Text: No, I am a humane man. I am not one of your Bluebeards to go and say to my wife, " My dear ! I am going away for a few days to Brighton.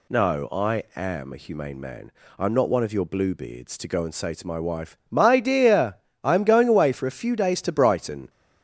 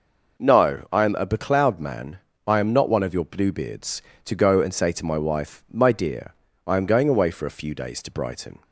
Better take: first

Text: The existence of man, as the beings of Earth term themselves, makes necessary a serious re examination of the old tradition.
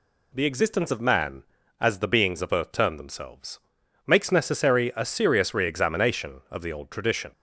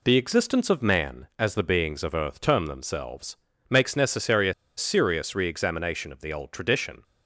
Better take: first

